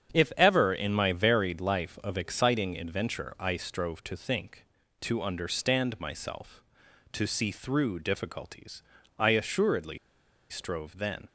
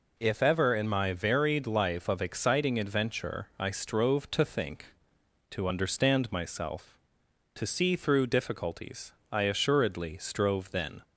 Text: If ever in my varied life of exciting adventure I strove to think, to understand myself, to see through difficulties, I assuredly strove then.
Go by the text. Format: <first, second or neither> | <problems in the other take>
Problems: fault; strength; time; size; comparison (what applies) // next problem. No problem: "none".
second | starts louder than the rest; strong; until 1.1 s; 8 dB // pauses between "assuredly" and "strove"; noticeable; at 9.9 s; 0.51 s long